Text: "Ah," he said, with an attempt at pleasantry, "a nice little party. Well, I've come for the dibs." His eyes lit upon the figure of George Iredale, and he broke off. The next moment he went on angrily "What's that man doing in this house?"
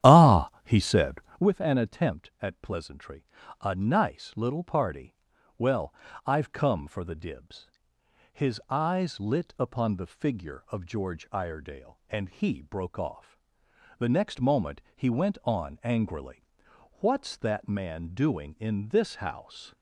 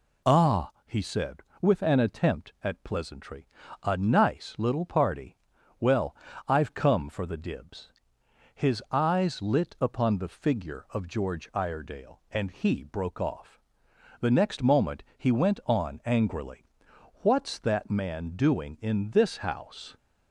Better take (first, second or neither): second